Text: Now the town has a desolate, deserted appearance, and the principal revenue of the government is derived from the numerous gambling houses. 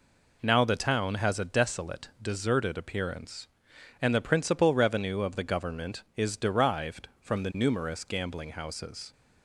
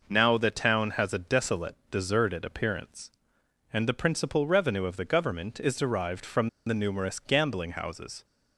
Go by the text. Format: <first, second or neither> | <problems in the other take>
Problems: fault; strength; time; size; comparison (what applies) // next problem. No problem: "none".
first | pauses between "from" and "the"; slight; at 6.4 s; 0.17 s long